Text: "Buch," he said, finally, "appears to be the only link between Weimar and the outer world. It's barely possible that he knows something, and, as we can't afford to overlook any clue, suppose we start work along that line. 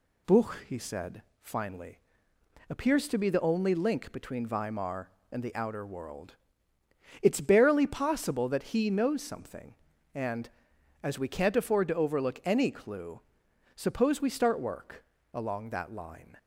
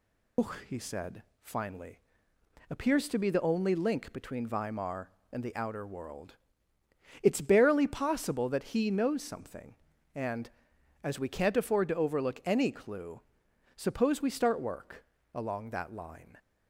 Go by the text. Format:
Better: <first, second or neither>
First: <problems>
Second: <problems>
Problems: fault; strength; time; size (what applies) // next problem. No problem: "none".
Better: first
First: pauses between "work" and "along"; slight; at 15.0 s; 0.26 s long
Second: loses the start of "Buch"; at 0.3 s; 120 ms // pauses between "work" and "along"; slight; at 15.0 s; 0.26 s long